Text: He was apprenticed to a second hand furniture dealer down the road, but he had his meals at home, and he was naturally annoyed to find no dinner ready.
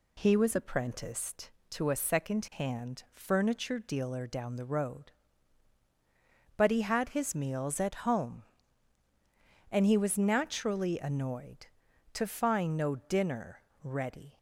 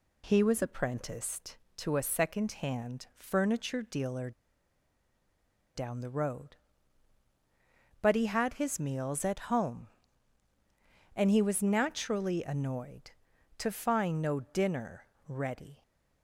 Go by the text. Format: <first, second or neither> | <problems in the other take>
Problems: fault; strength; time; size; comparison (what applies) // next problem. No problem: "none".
first | pauses between "dealer" and "down"; strong; at 4.3 s; 1.4 s long // pauses between "dinner" and "ready"; slight; at 15.0 s; 0.22 s long; slight in the first